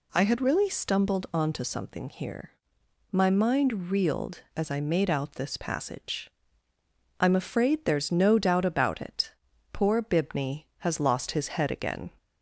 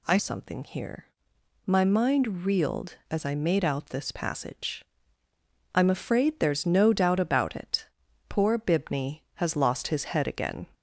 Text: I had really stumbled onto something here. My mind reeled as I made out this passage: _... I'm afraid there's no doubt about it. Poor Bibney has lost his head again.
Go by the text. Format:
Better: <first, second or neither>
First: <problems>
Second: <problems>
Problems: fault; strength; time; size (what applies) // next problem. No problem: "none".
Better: first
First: none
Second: skips "had really stumbled onto"; at 0.1 s